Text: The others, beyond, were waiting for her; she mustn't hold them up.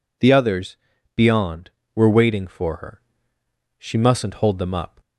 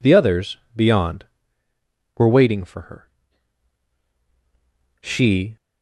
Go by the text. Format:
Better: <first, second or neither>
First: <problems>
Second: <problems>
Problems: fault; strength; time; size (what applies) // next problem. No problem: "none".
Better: first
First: none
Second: stops before "mustn't hold them up"; at 5.5 s